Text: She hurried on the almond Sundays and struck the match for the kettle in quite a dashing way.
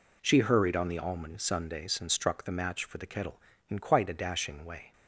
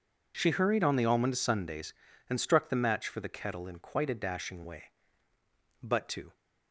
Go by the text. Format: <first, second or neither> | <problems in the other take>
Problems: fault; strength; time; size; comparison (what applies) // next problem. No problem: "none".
first | goes on to say "But to"; from 5.7 s on; 0.54 s long